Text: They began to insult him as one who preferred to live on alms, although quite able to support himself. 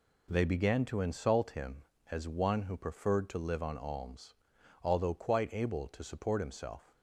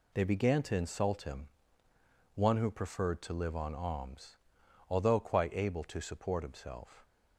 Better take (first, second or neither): first